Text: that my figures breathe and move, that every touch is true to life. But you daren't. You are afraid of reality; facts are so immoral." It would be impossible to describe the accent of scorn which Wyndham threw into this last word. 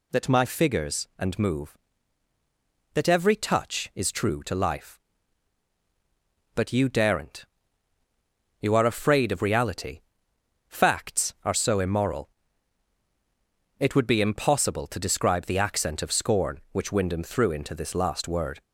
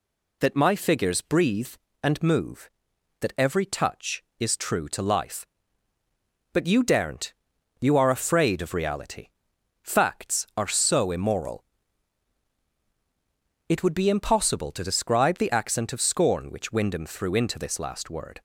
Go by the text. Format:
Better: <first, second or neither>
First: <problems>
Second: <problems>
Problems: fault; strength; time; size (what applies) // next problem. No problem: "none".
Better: second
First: skips "breathe"; at 1.1 s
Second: none